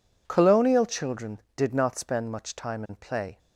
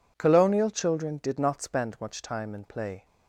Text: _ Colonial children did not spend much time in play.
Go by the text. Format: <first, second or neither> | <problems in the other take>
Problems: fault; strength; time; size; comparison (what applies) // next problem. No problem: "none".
neither | none